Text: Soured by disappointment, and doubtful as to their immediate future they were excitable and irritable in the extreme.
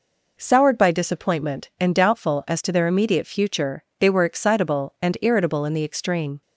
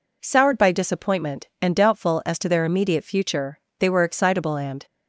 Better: first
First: pauses between "future" and "they"; slight; at 3.8 s; 0.16 s long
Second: pauses between "future" and "they"; slight; at 3.5 s; 0.20 s long // stops before "irritable in the extreme"; at 4.8 s

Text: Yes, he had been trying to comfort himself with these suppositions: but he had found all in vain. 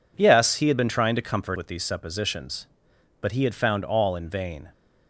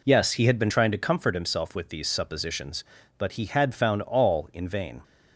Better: second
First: skips "himself"; at 1.5 s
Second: none

